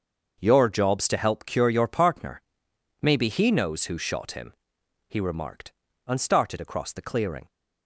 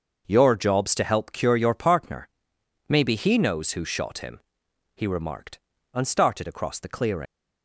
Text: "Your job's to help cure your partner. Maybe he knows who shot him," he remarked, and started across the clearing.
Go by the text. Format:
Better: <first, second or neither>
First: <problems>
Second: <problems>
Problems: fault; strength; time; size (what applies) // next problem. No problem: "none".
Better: first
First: starts louder than the rest; until 1.4 s; 6.5 dB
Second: starts louder than the rest; noticeable; until 1.2 s; 6 dB // leaves "clearing" unfinished; at 7.2 s; 105 ms